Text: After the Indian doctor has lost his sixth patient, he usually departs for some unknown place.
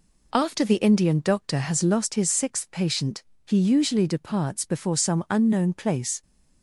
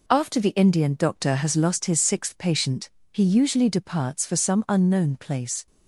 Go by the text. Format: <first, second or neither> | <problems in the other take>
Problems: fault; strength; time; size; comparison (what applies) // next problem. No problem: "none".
second | says "before" for "for"; at 4.6 s